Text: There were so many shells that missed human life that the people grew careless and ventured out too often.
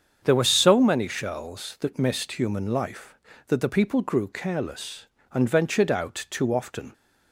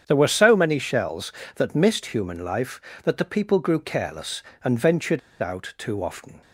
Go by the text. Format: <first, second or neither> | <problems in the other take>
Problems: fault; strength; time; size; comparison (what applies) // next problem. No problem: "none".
first | starts louder than the rest; strong; until 1.0 s; 8.5 dB; strong in the first // pauses between "ventured" and "out"; slight; at 5.1 s; 0.23 s long